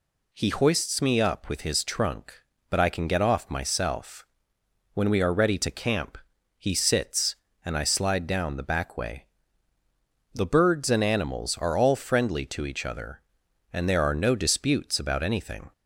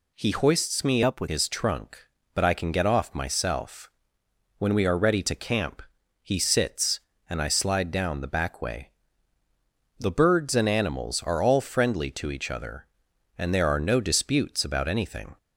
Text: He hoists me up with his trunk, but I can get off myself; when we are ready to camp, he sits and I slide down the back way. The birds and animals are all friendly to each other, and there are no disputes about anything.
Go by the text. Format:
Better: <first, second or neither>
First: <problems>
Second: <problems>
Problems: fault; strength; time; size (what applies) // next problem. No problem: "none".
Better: first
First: none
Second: changes voice from "up" to "with"; from 1.0 to 1.2 s; 0.2 s long